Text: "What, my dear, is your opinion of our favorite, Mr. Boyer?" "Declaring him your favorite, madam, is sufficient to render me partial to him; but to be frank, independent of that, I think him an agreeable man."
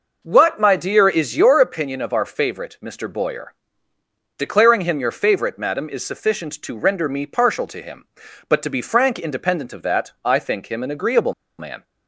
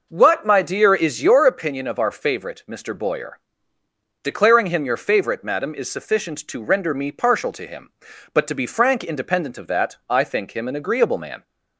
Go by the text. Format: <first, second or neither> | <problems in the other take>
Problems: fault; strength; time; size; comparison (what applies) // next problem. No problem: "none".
second | pauses between "agreeable" and "man"; slight; at 11.3 s; 0.26 s long